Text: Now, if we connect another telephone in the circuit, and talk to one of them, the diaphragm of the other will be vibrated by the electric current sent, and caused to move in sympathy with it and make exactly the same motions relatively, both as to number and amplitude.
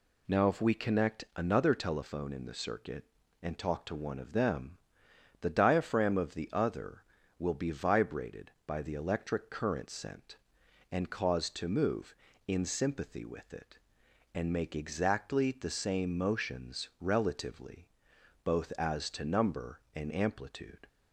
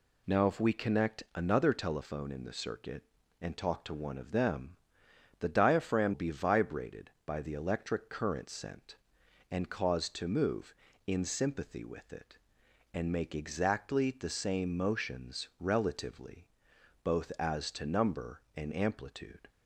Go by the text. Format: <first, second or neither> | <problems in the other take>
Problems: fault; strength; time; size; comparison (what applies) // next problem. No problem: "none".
first | skips "of the other will"; at 6.1 s